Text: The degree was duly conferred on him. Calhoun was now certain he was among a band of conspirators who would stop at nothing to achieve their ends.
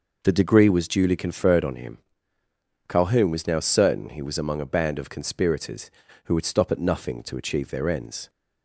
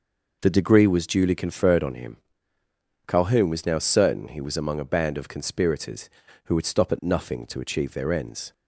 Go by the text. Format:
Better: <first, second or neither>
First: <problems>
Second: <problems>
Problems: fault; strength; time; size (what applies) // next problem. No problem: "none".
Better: neither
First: none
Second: none